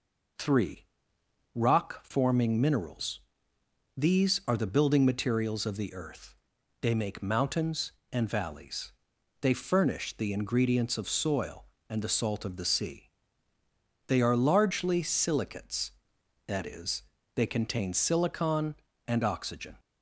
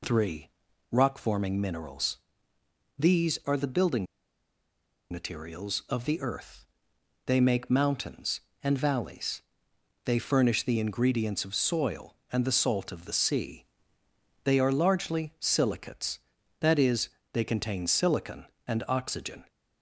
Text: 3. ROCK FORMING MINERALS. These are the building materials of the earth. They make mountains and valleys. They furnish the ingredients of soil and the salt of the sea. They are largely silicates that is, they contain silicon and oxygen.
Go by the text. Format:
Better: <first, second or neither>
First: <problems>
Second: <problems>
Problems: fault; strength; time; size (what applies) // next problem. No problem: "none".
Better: first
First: none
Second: pauses between "building" and "materials"; at 4.0 s; 1.0 s long